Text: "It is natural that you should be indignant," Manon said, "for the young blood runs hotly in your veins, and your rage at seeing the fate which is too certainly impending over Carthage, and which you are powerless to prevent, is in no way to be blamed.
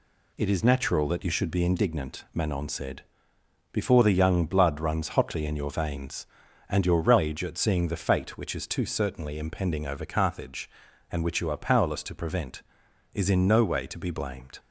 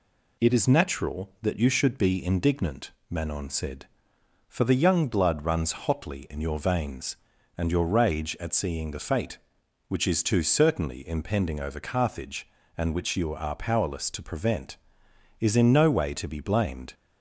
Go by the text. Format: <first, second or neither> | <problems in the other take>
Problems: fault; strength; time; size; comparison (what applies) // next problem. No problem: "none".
second | says "before" for "for"; at 3.7 s